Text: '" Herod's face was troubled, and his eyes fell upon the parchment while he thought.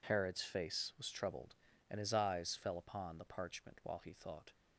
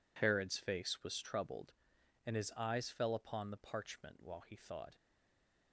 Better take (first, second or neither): first